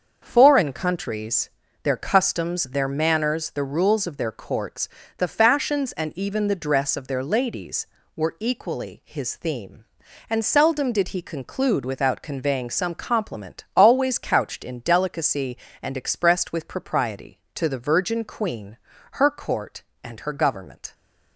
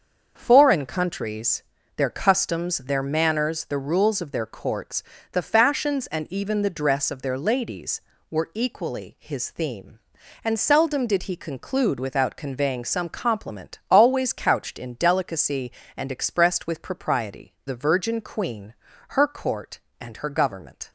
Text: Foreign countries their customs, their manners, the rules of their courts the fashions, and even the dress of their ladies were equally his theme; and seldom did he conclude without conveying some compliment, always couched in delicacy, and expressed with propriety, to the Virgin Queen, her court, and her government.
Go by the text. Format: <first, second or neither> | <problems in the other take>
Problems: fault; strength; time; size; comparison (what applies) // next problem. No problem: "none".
first | starts louder than the rest; until 1.3 s; 6.5 dB; also in the first // pauses between "countries" and "their"; slight; at 1.6 s; 0.34 s long; slight in the first // pauses between "courts" and "the"; slight; at 5.0 s; 0.30 s long; slight in the first // skips "to"; at 17.6 s